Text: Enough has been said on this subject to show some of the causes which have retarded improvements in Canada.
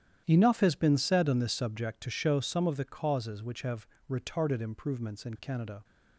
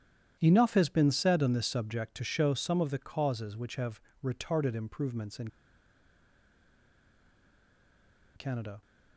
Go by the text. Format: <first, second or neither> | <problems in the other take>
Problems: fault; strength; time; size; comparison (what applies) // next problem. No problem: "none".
first | starts louder than the rest; strong; until 1.4 s; 10.5 dB; strong in the first // pauses between "have" and "retarded"; slight; at 3.9 s; 0.24 s long; slight in the first // pauses between "in" and "Canada"; strong; at 5.4 s; 2.8 s long